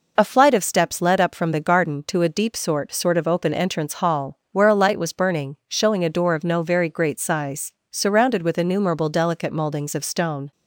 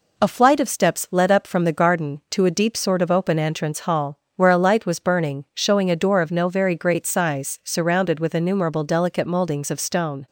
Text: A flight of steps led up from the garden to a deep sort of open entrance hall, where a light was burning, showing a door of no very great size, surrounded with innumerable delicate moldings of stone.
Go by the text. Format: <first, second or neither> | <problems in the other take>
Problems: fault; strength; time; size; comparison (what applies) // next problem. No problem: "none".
second | says "sort" twice; at 2.9 s